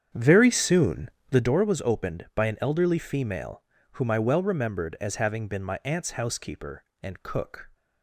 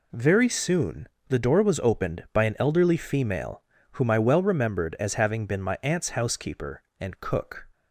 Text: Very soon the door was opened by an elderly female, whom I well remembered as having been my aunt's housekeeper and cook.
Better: second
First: starts louder than the rest; strong; until 1.6 s; 8.5 dB // pauses between "soon" and "the"; slight; at 1.0 s; 0.22 s long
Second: pauses between "soon" and "the"; slight; at 1.0 s; 0.22 s long

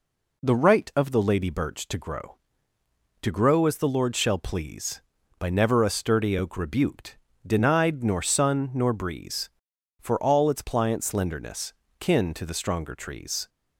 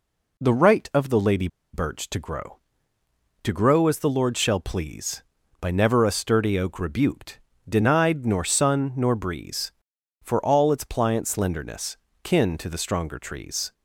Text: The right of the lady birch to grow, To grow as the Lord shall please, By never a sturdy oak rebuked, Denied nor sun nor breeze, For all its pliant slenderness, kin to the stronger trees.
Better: first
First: none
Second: pauses between "lady" and "birch"; slight; at 1.4 s; 0.26 s long

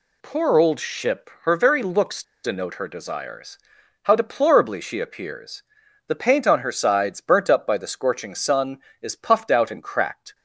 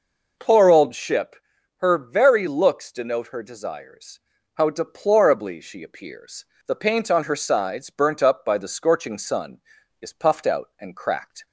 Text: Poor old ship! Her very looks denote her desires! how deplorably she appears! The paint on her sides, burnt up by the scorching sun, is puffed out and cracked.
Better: second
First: pauses between "looks" and "denote"; slight; at 2.2 s; 0.20 s long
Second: none

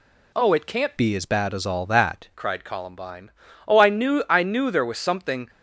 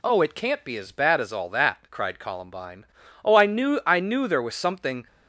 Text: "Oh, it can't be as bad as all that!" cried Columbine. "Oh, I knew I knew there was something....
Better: second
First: changes voice from "be" to "that"; from 0.9 to 2.2 s; 1.3 s long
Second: none

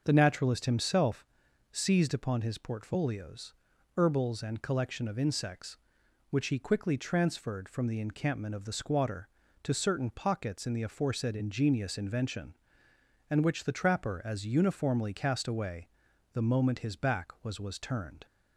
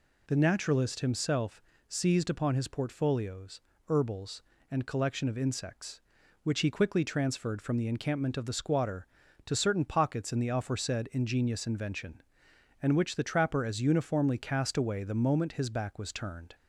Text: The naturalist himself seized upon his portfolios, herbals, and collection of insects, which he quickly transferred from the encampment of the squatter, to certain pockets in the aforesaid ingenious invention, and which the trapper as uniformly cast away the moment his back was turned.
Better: second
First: starts louder than the rest; until 1.0 s; 6.5 dB // pauses between "himself" and "seized"; noticeable; at 1.2 s; 0.46 s long // pauses between "away" and "the"; noticeable; at 15.8 s; 0.46 s long // says "was" twice; at 17.5 s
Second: pauses between "himself" and "seized"; slight; at 1.6 s; 0.26 s long

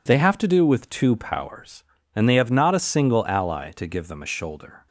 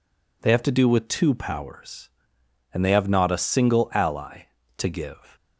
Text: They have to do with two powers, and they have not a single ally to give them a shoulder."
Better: first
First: none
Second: stops before "them a shoulder"; at 5.3 s

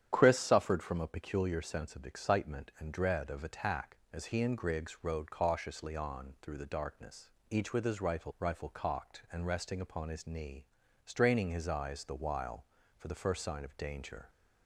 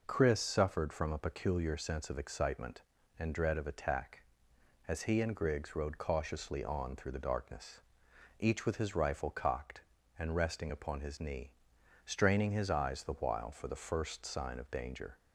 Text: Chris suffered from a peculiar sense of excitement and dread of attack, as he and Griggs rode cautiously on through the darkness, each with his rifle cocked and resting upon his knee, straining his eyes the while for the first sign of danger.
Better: second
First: starts louder than the rest; strong; until 1.1 s; 9.5 dB // says "rifle" twice; at 8.3 s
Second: none

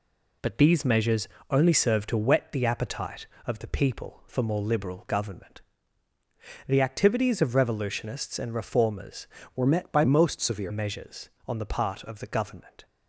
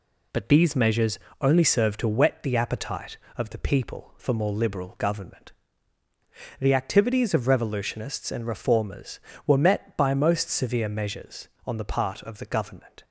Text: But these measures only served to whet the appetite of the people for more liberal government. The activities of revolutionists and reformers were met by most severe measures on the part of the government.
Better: second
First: pauses between "measures" and "only"; slight; at 1.2 s; 0.22 s long // changes voice from "were" to "severe"; from 9.5 to 10.7 s; 1.2 s long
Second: pauses between "measures" and "only"; slight; at 1.1 s; 0.22 s long

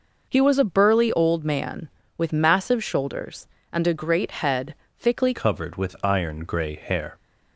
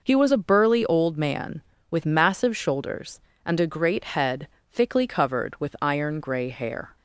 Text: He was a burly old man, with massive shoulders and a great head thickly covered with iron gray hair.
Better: second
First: pauses between "head" and "thickly"; slight; at 4.7 s; 0.24 s long // changes voice at "covered"; from 5.3 s on; 1.8 s long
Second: pauses between "head" and "thickly"; slight; at 4.4 s; 0.24 s long

